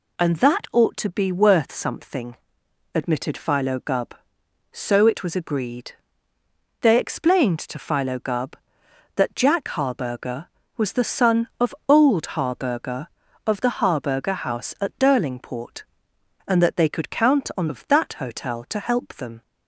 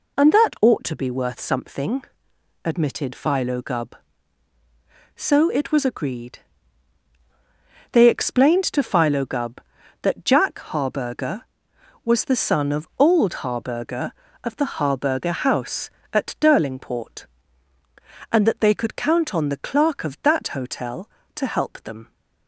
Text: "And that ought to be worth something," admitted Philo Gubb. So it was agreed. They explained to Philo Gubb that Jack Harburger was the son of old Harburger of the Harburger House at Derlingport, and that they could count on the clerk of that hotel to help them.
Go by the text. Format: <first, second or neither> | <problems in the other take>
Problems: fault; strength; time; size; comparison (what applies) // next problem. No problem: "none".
second | skips "the clerk"; at 17.6 s